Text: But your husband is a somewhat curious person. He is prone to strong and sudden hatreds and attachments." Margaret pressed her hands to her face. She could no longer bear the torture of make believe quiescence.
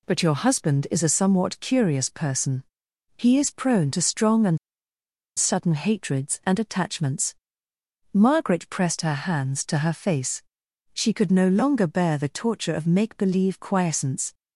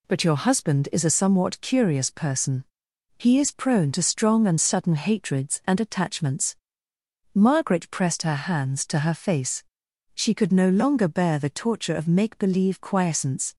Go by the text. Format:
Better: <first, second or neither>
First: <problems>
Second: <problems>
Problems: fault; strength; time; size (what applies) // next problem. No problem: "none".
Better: second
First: pauses between "and" and "sudden"; noticeable; at 4.5 s; 0.79 s long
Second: none